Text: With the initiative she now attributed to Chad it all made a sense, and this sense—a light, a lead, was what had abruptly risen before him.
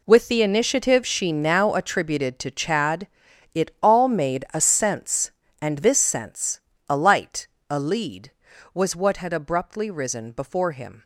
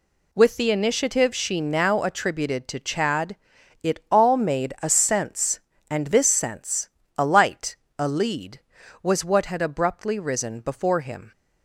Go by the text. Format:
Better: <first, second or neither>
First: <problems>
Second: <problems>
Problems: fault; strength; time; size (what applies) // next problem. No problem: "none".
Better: second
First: gets quieter; strong; throughout; 12.5 dB // pauses between "Chad" and "it"; noticeable; at 3.0 s; 0.48 s long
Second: pauses between "Chad" and "it"; noticeable; at 3.3 s; 0.48 s long